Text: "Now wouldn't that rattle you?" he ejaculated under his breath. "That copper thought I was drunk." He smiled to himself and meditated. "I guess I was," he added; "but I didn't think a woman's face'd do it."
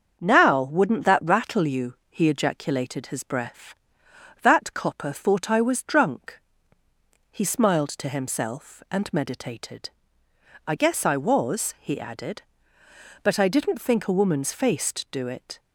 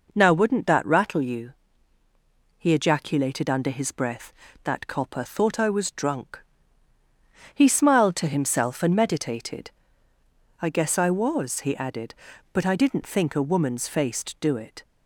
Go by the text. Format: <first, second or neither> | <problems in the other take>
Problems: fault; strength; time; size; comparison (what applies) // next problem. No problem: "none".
second | starts louder than the rest; until 1.2 s; 6.5 dB // skips "under"; at 3.0 s